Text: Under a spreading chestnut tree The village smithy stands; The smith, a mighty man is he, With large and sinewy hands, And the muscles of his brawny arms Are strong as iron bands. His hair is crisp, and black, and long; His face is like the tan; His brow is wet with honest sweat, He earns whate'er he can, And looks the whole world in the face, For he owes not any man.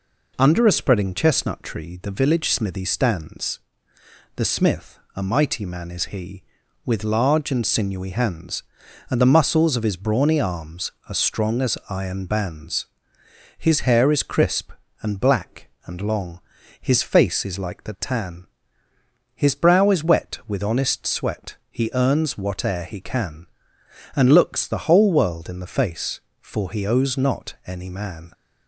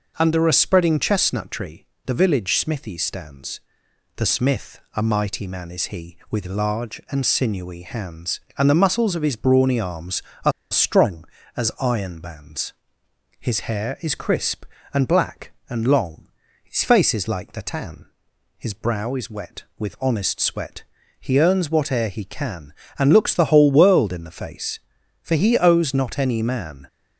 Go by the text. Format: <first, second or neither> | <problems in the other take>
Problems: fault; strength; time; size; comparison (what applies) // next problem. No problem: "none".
first | pauses between "tree" and "The"; slight; at 1.8 s; 0.20 s long // pauses between "Are" and "strong"; slight; at 10.5 s; 0.19 s long